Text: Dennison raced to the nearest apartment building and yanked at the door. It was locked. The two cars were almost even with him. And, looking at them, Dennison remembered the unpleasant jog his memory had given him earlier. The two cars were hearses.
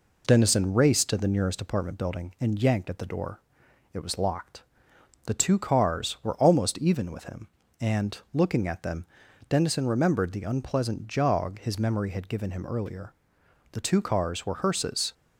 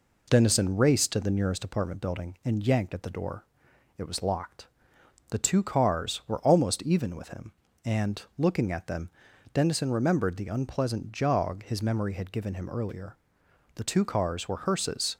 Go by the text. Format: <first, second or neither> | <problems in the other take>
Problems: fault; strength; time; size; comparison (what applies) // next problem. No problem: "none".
neither | none